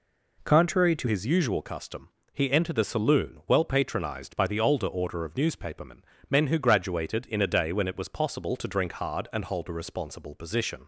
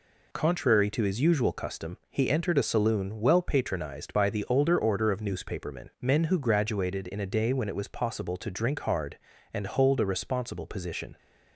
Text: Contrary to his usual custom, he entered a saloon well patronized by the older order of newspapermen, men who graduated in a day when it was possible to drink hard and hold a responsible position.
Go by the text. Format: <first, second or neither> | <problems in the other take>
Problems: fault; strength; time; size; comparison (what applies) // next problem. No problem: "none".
second | changes voice at "his"; from 1.0 s on; 9.8 s long